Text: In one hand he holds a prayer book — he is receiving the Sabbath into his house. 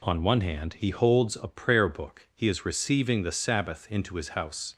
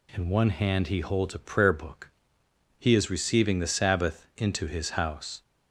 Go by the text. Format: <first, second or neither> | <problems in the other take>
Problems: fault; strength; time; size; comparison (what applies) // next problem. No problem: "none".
second | says "On" for "In"; at 0.0 s